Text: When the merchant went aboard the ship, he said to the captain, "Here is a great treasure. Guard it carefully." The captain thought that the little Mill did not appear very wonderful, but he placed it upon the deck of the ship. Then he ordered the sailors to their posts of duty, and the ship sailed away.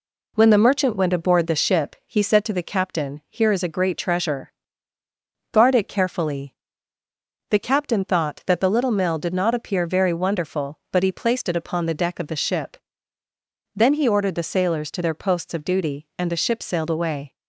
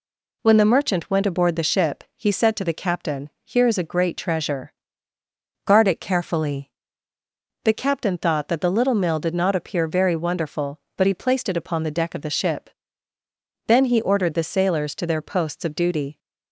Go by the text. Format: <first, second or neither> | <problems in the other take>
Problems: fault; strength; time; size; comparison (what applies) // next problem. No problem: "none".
first | stops before "and the ship sailed away"; at 16.1 s